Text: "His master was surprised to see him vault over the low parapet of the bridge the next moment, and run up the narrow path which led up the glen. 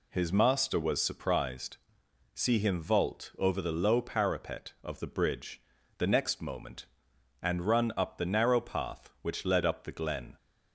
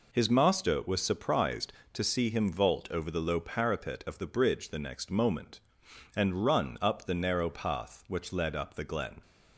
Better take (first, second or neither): second